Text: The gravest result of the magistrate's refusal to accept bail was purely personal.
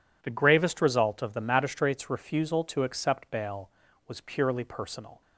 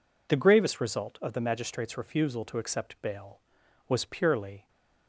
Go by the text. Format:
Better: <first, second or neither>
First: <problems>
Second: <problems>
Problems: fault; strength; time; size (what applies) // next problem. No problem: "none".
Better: first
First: none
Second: stops before "personal"; at 4.6 s